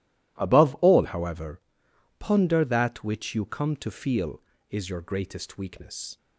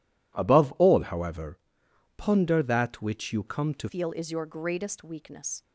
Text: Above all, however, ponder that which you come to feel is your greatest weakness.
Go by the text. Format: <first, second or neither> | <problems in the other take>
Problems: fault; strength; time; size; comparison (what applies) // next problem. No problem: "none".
first | changes voice at "feel"; from 3.8 s on; 1.8 s long